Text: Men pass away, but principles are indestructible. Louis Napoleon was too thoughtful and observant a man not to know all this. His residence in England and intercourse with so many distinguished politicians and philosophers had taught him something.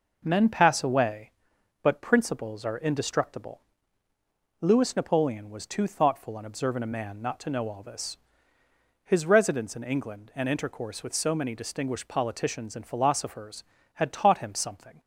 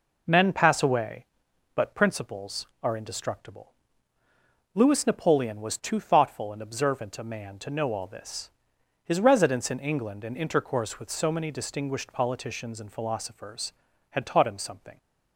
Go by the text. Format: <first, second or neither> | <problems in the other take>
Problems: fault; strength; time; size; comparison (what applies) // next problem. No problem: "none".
first | skips "not"; at 7.5 s